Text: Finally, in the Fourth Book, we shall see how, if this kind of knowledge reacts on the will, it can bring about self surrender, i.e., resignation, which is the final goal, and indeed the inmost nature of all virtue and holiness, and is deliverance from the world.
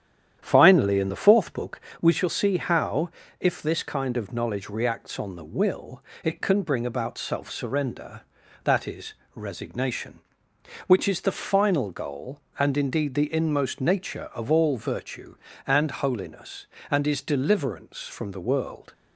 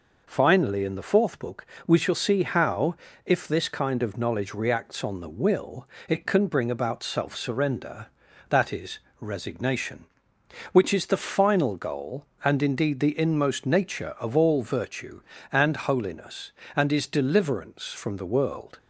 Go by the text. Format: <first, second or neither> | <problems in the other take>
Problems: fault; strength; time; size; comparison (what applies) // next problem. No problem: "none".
second | starts louder than the rest; strong; until 2.0 s; 10 dB